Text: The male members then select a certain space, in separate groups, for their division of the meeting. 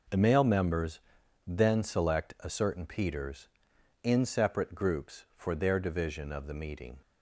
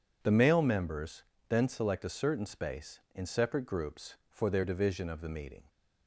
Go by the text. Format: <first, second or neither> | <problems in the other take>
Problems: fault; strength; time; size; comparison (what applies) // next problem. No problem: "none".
second | pauses between "members" and "then"; noticeable; at 1.0 s; 0.46 s long; slight in the second // says "peters" for "space"; at 2.8 s